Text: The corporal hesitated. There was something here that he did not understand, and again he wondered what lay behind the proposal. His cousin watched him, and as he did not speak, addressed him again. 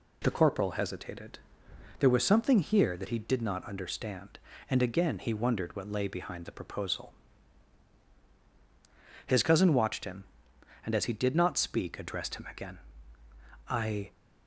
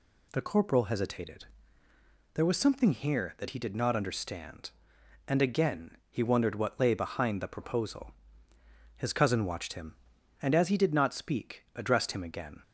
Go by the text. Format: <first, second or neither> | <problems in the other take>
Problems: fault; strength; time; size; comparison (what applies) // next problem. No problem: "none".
second | goes on to say "I"; slight; from 13.6 s on; 0.44 s long